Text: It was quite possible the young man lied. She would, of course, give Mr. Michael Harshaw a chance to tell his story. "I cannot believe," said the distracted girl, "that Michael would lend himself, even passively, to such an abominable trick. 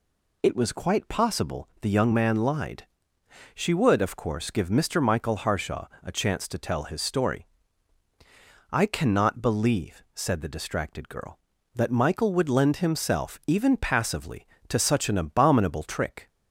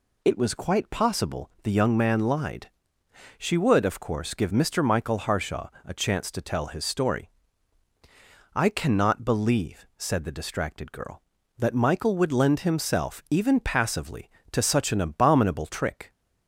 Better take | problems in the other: neither | pauses between "Harshaw" and "a"; slight; the same in both

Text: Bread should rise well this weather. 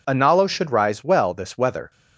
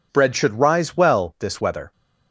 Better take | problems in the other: second | says "Analo" for "Bread"; at 0.0 s

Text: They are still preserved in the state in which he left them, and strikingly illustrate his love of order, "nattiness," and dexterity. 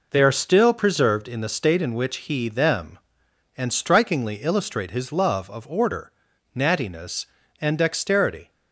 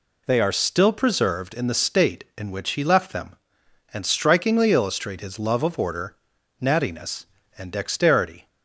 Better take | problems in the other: second | skips "left"; at 2.4 s

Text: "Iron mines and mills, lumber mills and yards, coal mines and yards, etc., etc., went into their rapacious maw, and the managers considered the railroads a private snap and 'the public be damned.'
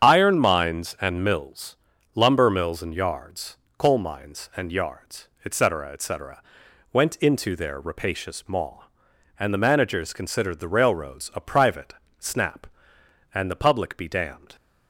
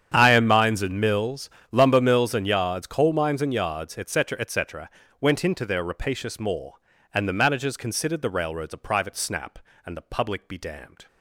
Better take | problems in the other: second | loses the start of "Iron"; at 0.0 s; 70 ms // starts louder than the rest; strong; until 1.0 s; 8 dB; strong in the second // pauses between "private" and "snap"; slight; at 11.9 s; 0.24 s long

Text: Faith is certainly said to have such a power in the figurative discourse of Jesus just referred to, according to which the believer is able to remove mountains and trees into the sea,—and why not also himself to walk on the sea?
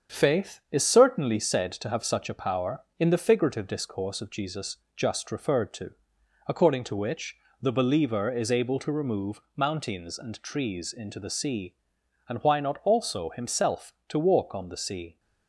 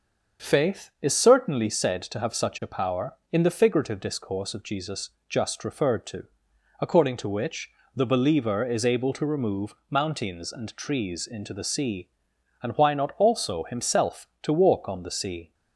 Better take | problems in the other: second | gets quieter; noticeable; throughout; 5 dB // starts louder than the rest; strong; until 1.2 s; 7.5 dB; also in the second // pauses between "Jesus" and "just"; slight; at 4.7 s; 0.18 s long; slight in the second // pauses between "which" and "the"; slight; at 7.3 s; 0.26 s long; slight in the second // pauses between "remove" and "mountains"; slight; at 9.3 s; 0.16 s long; slight in the second

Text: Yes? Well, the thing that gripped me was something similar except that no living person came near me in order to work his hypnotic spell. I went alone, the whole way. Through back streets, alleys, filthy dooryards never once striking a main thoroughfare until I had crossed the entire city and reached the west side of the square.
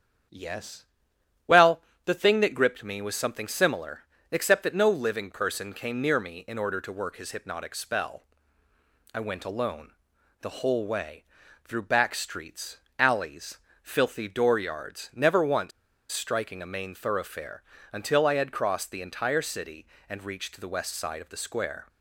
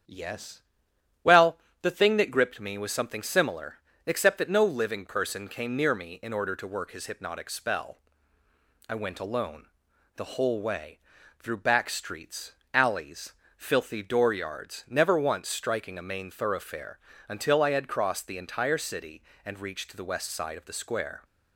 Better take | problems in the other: second | starts louder than the rest; strong; until 2.1 s; 8.5 dB; strong in the second // pauses between "similar" and "except"; slight; at 4.0 s; 0.28 s long; slight in the second // pauses between "once" and "striking"; at 15.7 s; 0.41 s long // pauses between "thoroughfare" and "until"; slight; at 17.6 s; 0.32 s long; slight in the second

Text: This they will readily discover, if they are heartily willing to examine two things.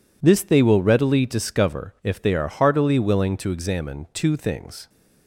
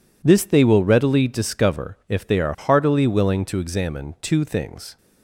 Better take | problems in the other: neither | none

